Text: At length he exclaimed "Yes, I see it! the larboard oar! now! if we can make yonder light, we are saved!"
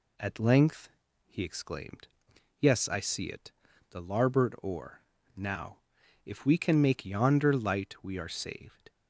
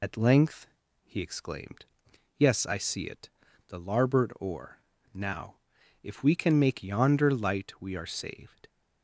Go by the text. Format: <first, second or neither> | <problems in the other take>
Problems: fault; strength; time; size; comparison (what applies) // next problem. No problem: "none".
first | loses the start of "At"; at 0.0 s; 70 ms // pauses between "length" and "he"; at 0.6 s; 0.38 s long; also in the first // pauses between "exclaimed" and "Yes"; noticeable; at 1.8 s; 0.52 s long; noticeable in the first